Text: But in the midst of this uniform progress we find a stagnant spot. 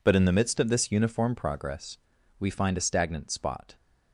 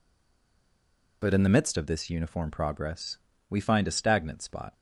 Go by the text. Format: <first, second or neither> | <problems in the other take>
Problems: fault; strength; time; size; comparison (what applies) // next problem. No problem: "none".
first | stays silent before the first word; noticeable; until 1.2 s; 1.2 s long // pauses between "progress" and "we"; slight; at 3.1 s; 0.32 s long; also in the first